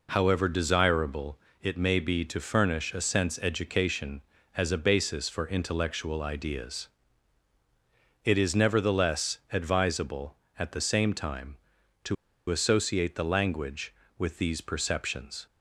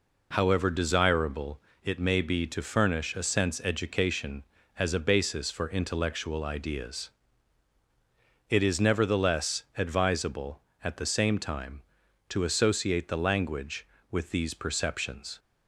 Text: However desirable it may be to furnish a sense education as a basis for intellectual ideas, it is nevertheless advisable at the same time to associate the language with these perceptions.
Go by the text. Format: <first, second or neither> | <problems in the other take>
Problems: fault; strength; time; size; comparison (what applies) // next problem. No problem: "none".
second | pauses between "desirable" and "it"; slight; at 1.3 s; 0.24 s long; slight in the second // pauses between "to" and "associate"; slight; at 12.1 s; 0.34 s long